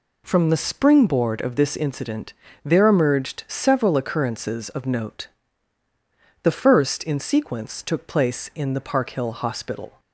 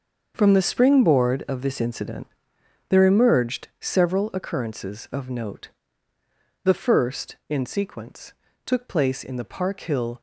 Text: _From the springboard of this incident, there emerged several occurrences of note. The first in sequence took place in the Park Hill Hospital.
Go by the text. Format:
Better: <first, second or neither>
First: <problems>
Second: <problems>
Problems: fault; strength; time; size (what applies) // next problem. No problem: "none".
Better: first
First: none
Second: starts louder than the rest; until 1.3 s; 6.5 dB // pauses between "sequence" and "took"; slight; at 8.3 s; 0.32 s long // stops before "Hospital"; at 10.1 s